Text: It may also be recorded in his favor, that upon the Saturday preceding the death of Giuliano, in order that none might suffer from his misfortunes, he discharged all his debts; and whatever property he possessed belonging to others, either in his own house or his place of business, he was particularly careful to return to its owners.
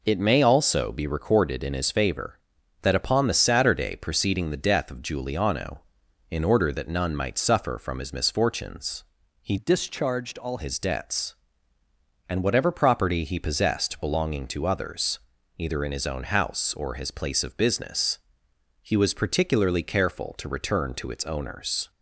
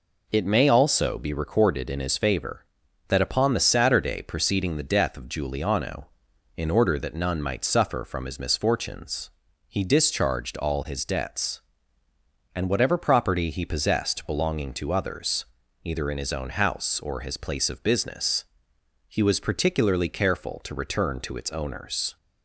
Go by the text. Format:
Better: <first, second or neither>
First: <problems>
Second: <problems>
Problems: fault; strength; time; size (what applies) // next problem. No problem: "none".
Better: second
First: changes voice from "discharged" to "all"; from 9.5 to 10.5 s; 1.0 s long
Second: none